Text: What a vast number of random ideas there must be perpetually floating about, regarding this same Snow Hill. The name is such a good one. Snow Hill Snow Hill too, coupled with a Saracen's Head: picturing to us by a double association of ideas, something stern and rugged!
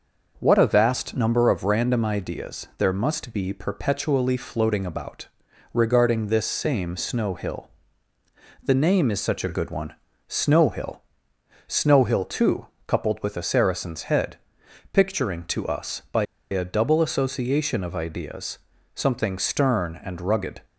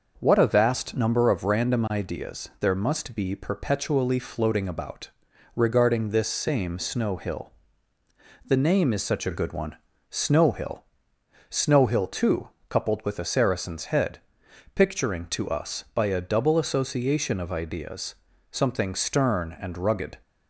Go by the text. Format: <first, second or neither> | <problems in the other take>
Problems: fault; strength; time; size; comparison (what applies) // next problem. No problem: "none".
second | pauses between "Hill" and "Snow"; noticeable; at 11.0 s; 0.68 s long; noticeable in the second // pauses between "by" and "a"; slight; at 16.2 s; 0.26 s long